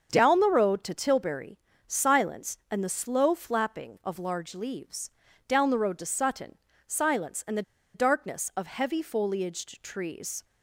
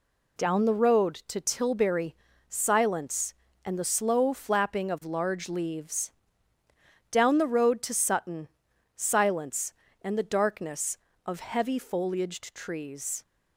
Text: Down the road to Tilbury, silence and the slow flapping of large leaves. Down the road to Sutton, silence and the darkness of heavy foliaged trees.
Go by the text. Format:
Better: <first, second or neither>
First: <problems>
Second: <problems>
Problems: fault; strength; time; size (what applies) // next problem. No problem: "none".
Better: second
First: starts louder than the rest; until 1.1 s; 6.5 dB // pauses between "the" and "darkness"; slight; at 7.6 s; 0.31 s long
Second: none